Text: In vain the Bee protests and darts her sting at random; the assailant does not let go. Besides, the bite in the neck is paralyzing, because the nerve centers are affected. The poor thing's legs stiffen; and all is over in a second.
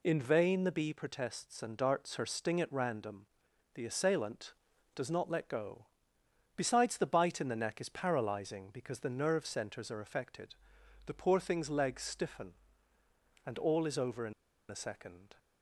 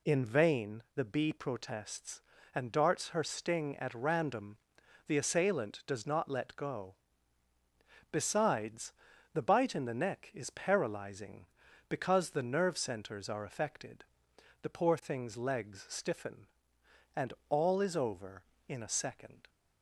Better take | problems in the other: second | pauses between "in" and "a"; at 14.3 s; 0.36 s long

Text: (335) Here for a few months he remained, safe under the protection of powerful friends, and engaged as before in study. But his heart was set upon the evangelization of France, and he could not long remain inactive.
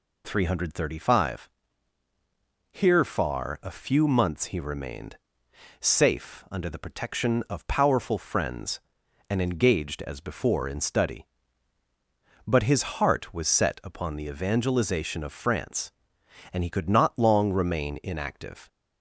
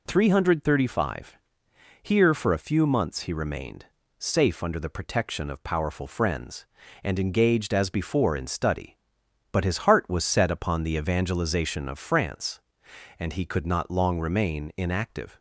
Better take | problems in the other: second | says "far" for "for"; at 3.0 s // pauses between "his" and "heart"; slight; at 12.8 s; 0.16 s long

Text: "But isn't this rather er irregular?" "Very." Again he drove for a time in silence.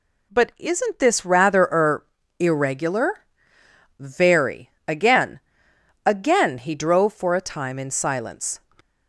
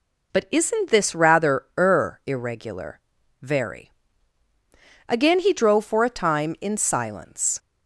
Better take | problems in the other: second | pauses between "er" and "irregular"; slight; at 2.0 s; 0.32 s long // says "Again" twice; at 6.0 s

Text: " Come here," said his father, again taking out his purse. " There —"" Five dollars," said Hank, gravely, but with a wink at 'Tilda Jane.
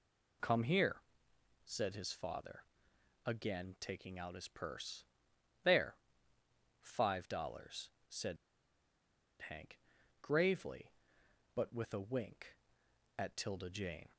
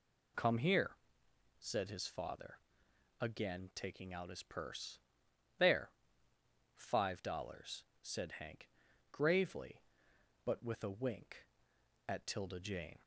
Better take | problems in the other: second | pauses between "said" and "Hank"; at 8.3 s; 1.0 s long

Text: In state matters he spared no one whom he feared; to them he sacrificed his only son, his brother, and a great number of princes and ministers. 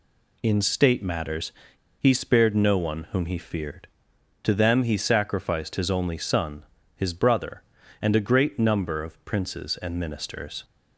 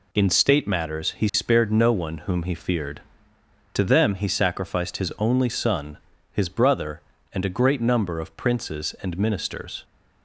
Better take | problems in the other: second | pauses between "matters" and "he"; noticeable; at 1.5 s; 0.50 s long

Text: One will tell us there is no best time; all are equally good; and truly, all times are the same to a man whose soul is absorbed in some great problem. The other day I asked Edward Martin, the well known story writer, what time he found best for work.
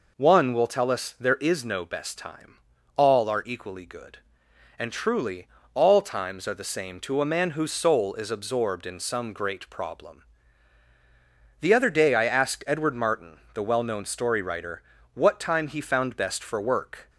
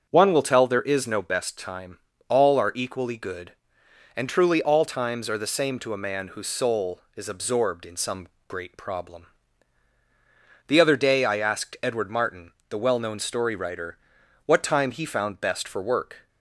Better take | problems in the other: first | starts louder than the rest; until 1.1 s; 6.5 dB // skips "us"; at 0.6 s // pauses between "some" and "great"; slight; at 8.2 s; 0.20 s long

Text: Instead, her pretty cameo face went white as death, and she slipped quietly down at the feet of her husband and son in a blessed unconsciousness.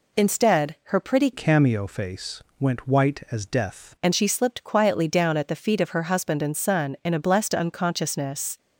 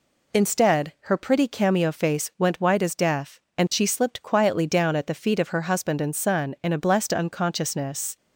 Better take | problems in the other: second | changes voice from "cameo" to "death"; from 1.3 to 3.9 s; 2.6 s long // pauses between "face" and "went"; slight; at 2.4 s; 0.16 s long

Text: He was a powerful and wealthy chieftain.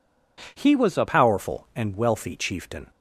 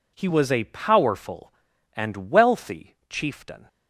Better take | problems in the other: second | changes voice at "powerful"; from 1.0 s on; 1.9 s long

